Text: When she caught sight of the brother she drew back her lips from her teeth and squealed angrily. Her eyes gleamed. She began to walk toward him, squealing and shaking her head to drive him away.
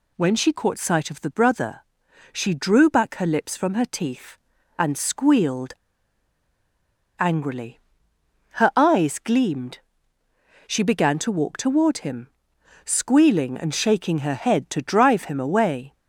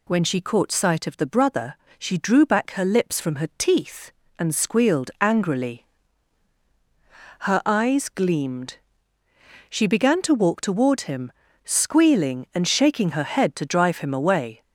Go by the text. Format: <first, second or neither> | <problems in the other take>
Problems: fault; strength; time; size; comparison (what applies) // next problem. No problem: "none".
second | pauses between "brother" and "she"; noticeable; at 1.8 s; 0.50 s long; slight in the second // pauses between "squealed" and "angrily"; strong; at 5.7 s; 1.4 s long